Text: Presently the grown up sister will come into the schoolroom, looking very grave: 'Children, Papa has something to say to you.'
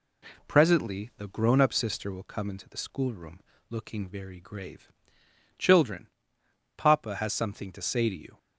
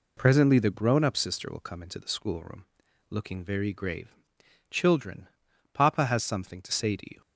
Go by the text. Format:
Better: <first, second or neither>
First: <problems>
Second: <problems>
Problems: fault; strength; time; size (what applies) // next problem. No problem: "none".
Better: neither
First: none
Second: none